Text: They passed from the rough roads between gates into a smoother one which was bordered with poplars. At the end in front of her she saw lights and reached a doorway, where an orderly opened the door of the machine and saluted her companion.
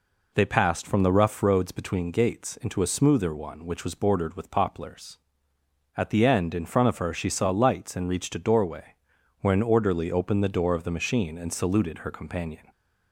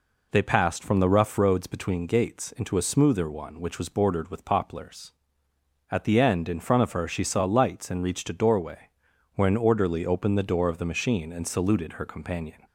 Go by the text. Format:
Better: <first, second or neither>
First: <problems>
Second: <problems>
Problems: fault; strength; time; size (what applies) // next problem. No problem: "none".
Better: neither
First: none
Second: none